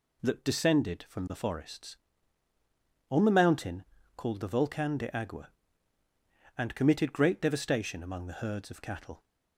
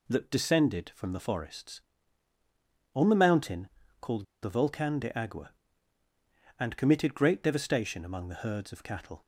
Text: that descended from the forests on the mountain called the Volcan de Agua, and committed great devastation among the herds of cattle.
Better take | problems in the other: first | pauses between "mountain" and "called"; slight; at 3.6 s; 0.32 s long; slight in the first // pauses between "called" and "the"; slight; at 4.2 s; 0.18 s long

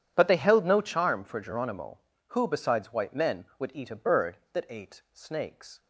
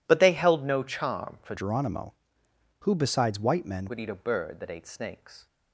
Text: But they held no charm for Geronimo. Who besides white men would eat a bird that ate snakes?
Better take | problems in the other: first | changes voice from "Geronimo" to "men"; from 1.5 to 3.8 s; 2.3 s long

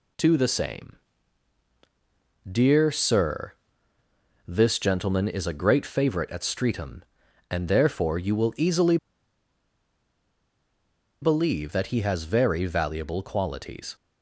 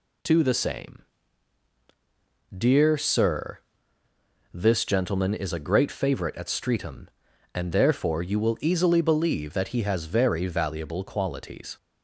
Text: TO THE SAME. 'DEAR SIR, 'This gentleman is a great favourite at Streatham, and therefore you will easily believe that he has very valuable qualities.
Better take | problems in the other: second | pauses between "easily" and "believe"; strong; at 8.9 s; 2.2 s long

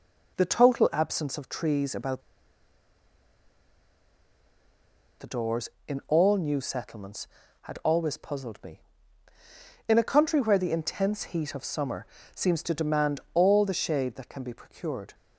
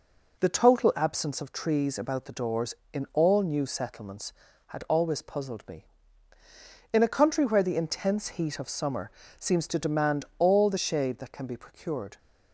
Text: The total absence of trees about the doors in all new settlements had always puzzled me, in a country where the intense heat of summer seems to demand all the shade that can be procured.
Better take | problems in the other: second | pauses between "about" and "the"; strong; at 2.2 s; 2.9 s long // pauses between "summer" and "seems"; slight; at 12.0 s; 0.28 s long; slight in the second

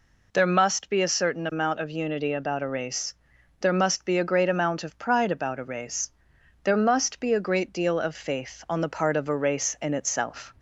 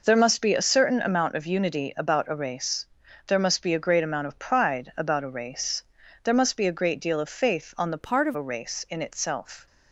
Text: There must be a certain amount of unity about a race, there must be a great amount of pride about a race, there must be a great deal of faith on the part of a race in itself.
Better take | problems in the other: first | changes voice from "part" to "of"; from 8.0 to 8.3 s; 0.3 s long

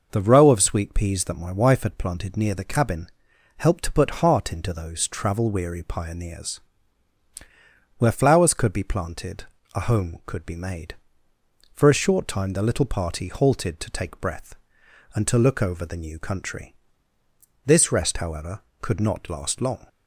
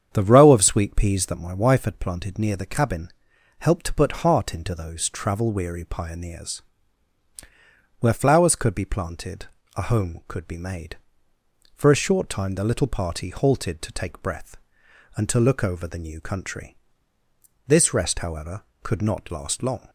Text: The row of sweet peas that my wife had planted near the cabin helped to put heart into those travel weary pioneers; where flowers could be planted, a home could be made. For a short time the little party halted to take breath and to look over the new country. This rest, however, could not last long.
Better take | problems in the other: first | starts louder than the rest; strong; until 1.4 s; 8 dB // pauses between "cabin" and "helped"; noticeable; at 3.0 s; 0.50 s long; noticeable in the first

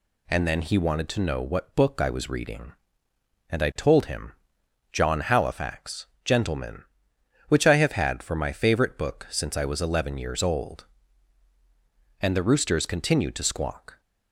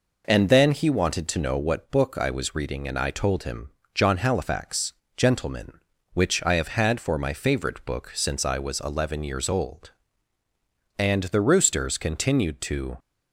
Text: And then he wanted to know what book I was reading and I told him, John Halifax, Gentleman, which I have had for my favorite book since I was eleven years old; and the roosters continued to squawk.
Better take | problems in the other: first | stops before "squawk"; at 12.9 s

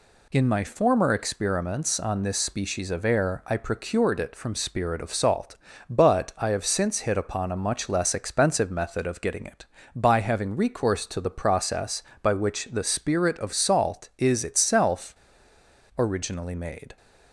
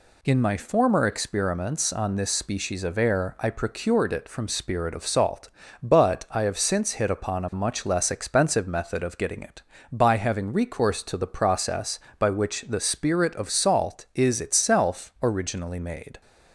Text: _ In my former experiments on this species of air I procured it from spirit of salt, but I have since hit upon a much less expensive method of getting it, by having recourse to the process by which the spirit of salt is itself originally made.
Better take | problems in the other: second | pauses between "itself" and "originally"; noticeable; at 15.1 s; 0.80 s long

